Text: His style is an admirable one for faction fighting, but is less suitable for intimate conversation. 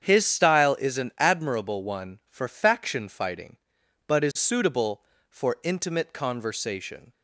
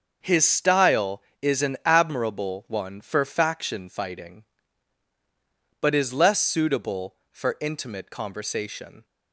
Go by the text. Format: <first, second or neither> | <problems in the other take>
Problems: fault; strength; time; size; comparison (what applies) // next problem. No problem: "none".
second | starts louder than the rest; strong; until 1.0 s; 8 dB; also in the second // skips "less"; at 4.3 s